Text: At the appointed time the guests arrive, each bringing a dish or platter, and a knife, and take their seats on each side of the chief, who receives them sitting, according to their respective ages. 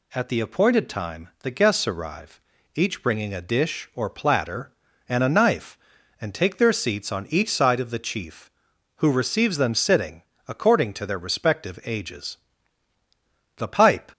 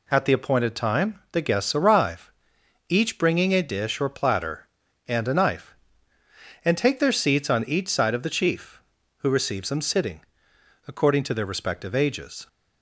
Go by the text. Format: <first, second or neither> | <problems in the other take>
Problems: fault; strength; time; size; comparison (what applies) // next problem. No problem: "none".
second | goes on to say "The pipe"; from 13.5 s on; 0.56 s long